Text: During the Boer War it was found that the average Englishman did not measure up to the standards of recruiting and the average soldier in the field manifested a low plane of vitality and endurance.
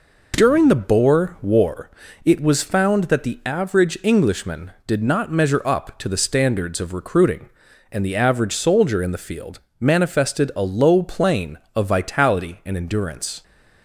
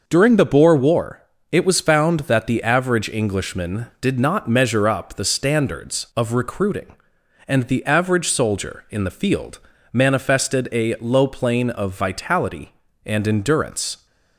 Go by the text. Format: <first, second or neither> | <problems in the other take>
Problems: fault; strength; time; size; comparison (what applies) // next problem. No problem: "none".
first | pauses between "War" and "it"; slight; at 1.2 s; 0.30 s long; slight in the first // skips "to"; at 5.1 s // pauses between "field" and "manifested"; slight; at 9.5 s; 0.32 s long; slight in the first